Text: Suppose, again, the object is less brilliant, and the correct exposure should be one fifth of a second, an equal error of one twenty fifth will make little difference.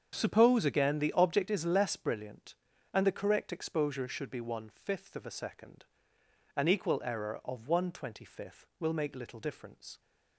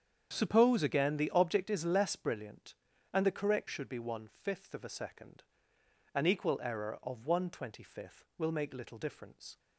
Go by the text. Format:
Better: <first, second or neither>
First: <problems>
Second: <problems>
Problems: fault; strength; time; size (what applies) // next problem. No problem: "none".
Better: first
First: starts louder than the rest; strong; until 1.1 s; 7.5 dB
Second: starts louder than the rest; strong; until 1.3 s; 8 dB // skips "exposure"; at 3.6 s